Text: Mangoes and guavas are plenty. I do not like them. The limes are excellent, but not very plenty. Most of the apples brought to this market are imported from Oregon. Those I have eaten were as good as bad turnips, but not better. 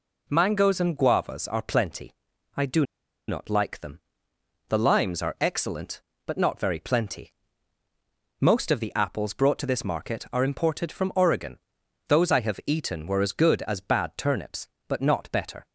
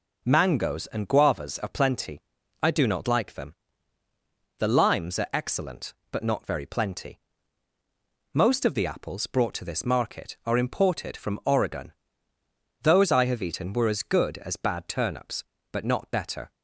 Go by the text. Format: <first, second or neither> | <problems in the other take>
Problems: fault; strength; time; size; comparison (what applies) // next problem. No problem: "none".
second | pauses between "do" and "not"; at 2.8 s; 0.45 s long